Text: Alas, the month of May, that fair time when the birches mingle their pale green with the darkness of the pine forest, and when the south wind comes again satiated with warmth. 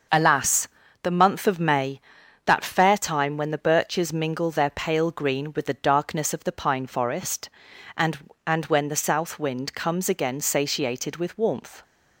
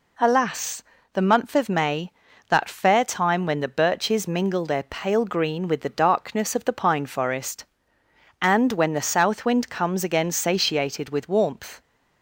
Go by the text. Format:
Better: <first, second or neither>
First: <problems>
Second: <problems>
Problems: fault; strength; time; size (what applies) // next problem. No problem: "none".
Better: second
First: starts louder than the rest; noticeable; until 1.4 s; 6 dB // says "and" twice; at 8.4 s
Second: none